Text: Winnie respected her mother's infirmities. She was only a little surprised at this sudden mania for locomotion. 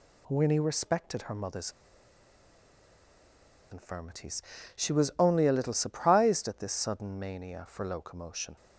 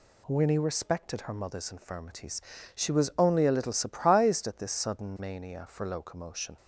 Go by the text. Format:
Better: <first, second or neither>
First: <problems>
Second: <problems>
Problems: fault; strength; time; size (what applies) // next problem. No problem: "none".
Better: second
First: pauses between "mother's" and "infirmities"; strong; at 1.7 s; 1.9 s long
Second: none